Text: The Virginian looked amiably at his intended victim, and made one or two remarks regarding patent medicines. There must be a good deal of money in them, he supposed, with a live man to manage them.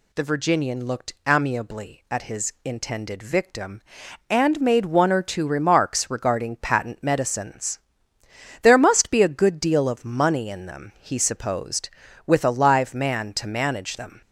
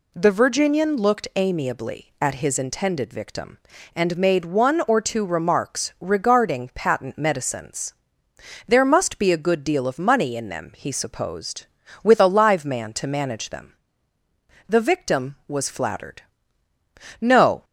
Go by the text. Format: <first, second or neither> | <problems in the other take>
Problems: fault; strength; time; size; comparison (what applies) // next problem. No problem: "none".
first | goes on to say "The victim was flattered No"; strong; from 14.6 s on; 2.9 s long